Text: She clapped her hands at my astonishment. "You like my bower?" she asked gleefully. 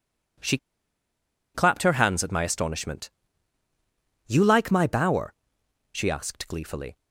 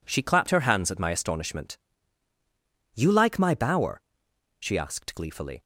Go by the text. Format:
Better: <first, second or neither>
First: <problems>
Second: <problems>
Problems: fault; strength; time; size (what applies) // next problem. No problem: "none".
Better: second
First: pauses between "She" and "clapped"; noticeable; at 0.5 s; 0.98 s long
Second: none